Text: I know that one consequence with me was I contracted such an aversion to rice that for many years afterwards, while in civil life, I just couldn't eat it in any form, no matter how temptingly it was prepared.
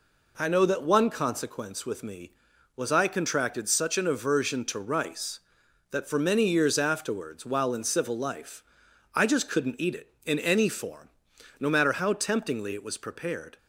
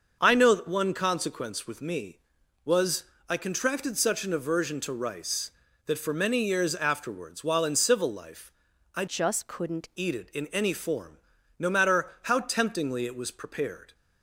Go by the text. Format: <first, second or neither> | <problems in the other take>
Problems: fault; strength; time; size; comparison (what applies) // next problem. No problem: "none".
first | starts louder than the rest; until 1.2 s; 6.5 dB // pauses between "was" and "I"; slight; at 3.0 s; 0.24 s long // changes voice from "just" to "couldn't"; from 9.0 to 9.9 s; 0.9 s long